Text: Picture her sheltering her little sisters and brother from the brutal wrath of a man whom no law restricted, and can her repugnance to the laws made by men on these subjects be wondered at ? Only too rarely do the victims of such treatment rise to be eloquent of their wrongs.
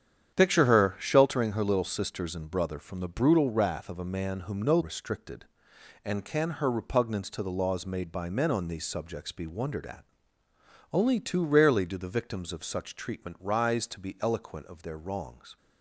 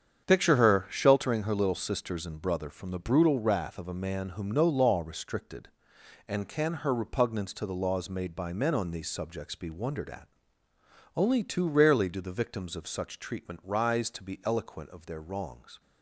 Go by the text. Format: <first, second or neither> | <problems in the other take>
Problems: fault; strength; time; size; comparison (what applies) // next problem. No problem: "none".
second | starts louder than the rest; strong; until 1.3 s; 9 dB; strong in the second // skips "law"; at 4.7 s